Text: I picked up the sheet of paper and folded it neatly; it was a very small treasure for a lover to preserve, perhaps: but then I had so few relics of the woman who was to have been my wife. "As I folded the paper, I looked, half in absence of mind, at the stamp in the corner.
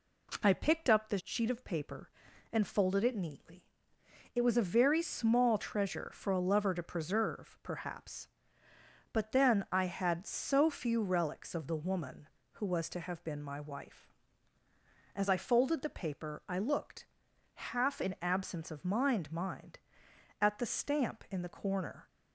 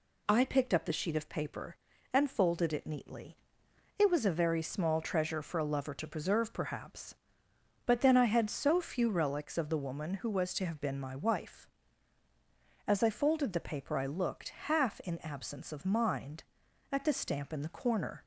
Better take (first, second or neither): second